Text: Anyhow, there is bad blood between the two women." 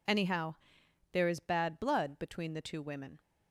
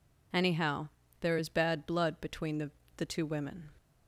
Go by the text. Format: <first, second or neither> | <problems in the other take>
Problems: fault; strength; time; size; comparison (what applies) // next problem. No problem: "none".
first | says "the" twice; at 2.9 s